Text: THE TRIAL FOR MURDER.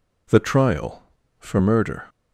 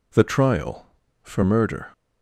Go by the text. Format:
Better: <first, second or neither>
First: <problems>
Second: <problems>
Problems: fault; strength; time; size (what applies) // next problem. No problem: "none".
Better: neither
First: none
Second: none